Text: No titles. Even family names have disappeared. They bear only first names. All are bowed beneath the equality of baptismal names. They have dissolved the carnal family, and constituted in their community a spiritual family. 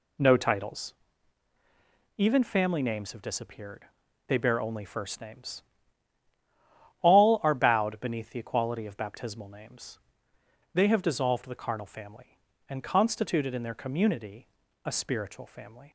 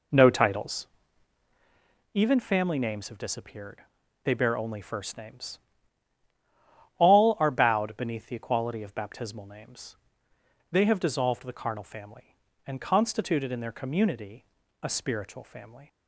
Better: first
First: pauses between "community" and "a"; slight; at 14.4 s; 0.36 s long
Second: starts louder than the rest; until 1.8 s; 3.5 dB // pauses between "community" and "a"; slight; at 14.4 s; 0.36 s long

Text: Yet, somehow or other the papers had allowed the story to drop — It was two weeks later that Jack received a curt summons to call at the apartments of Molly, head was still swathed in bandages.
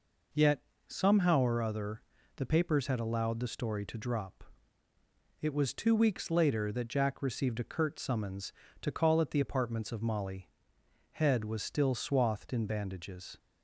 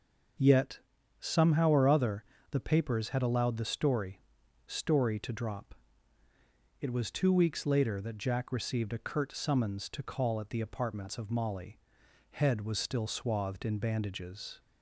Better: first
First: pauses between "other" and "the"; slight; at 2.0 s; 0.36 s long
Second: starts louder than the rest; until 1.8 s; 6.5 dB // pauses between "other" and "the"; slight; at 2.2 s; 0.29 s long // says "story" twice; at 4.6 s

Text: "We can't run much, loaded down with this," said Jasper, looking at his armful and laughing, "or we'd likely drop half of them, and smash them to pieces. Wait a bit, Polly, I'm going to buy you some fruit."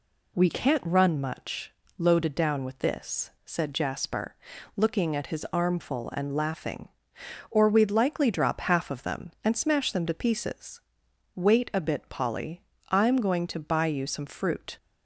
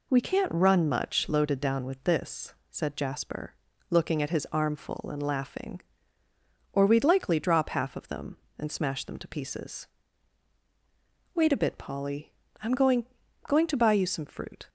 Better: first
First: none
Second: says "going" twice; at 13.4 s

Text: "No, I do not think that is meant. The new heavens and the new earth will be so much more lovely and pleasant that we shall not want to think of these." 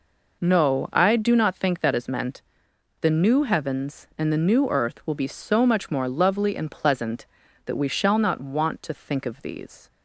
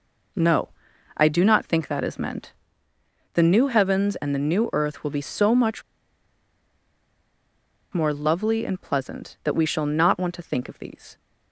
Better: first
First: none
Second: pauses between "much" and "more"; strong; at 5.8 s; 2.1 s long

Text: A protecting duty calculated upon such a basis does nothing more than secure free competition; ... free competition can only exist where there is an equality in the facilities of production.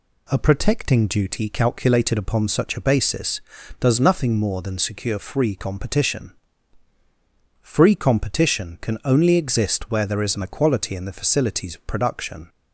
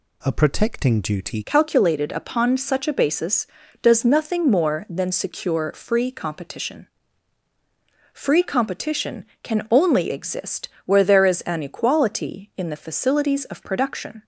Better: first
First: none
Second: changes voice at "calculated"; from 1.4 s on; 12.8 s long // pauses between "exist" and "where"; slight; at 10.6 s; 0.18 s long

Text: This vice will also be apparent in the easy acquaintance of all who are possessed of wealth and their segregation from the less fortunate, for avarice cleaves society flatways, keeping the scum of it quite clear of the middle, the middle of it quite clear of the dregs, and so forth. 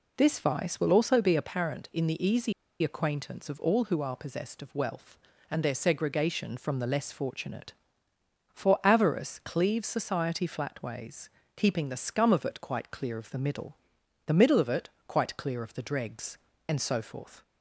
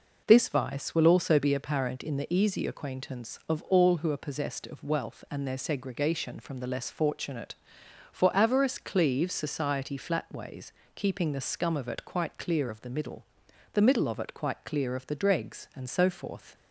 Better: second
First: pauses between "easy" and "acquaintance"; slight; at 2.5 s; 0.29 s long // pauses between "it" and "quite"; slight; at 14.8 s; 0.18 s long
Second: none

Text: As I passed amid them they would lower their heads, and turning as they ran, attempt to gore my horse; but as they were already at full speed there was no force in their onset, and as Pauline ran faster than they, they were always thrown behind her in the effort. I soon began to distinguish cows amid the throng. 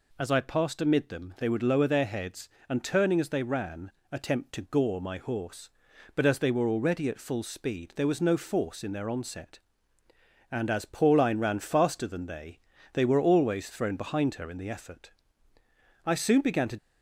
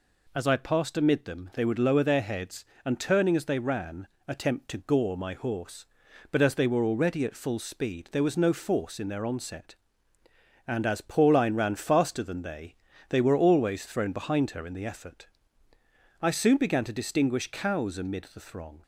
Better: second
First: stops before "distinguish cows amid the throng"; at 16.7 s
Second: none

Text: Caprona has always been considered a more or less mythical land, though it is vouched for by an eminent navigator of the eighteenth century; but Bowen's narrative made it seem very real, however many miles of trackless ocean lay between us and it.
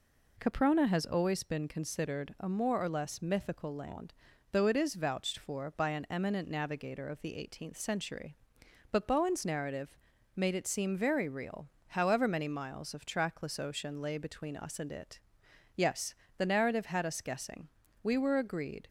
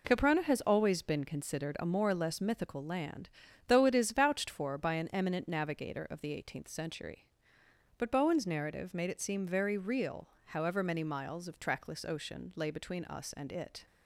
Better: second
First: pauses between "narrative" and "made"; at 9.9 s; 0.38 s long // goes on to say "Yes the narrative had us guessing We were agreed"; strong; from 15.7 s on; 3.1 s long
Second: none

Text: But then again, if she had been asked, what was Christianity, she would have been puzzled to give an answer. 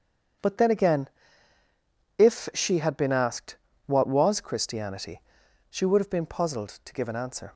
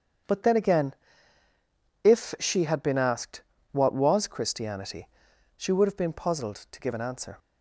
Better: neither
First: starts louder than the rest; strong; until 2.5 s; 7.5 dB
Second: starts louder than the rest; strong; until 2.4 s; 7.5 dB

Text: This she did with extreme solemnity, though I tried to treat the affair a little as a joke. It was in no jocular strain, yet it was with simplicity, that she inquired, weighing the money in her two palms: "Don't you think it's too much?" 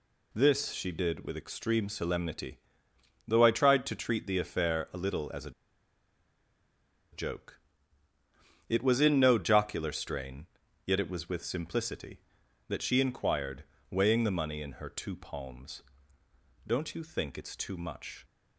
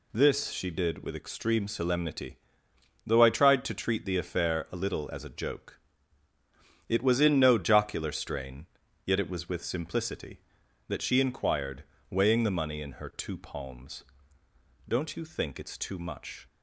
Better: second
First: pauses between "a" and "joke"; strong; at 5.5 s; 1.6 s long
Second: none

